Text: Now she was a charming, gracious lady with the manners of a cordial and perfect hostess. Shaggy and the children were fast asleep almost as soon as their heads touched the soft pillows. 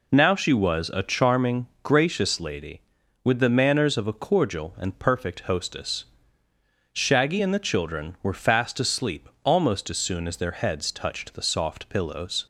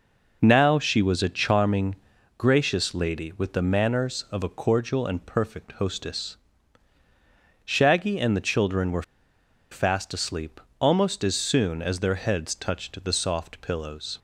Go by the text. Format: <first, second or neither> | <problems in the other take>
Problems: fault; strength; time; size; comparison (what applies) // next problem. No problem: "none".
first | pauses between "were" and "fast"; noticeable; at 9.0 s; 0.69 s long // pauses between "asleep" and "almost"; slight; at 10.6 s; 0.20 s long